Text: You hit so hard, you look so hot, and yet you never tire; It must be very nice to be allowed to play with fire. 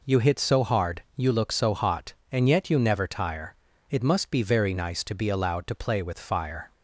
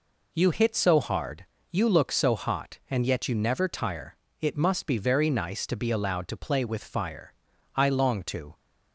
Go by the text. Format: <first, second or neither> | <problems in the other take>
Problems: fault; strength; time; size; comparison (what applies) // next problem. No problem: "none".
first | goes on to say "I long to"; noticeable; from 7.7 s on; 0.78 s long